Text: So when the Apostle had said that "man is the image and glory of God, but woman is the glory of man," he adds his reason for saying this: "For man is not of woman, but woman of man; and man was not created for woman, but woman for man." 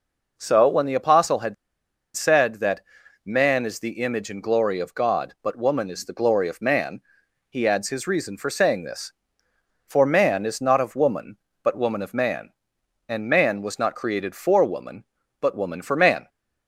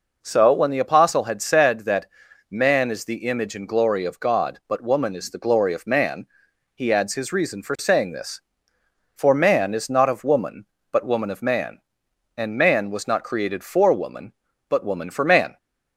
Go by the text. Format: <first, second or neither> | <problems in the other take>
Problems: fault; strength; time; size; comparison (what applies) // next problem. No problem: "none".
second | pauses between "had" and "said"; noticeable; at 1.5 s; 0.61 s long // pauses between "that" and "man"; at 2.8 s; 0.44 s long; also in the second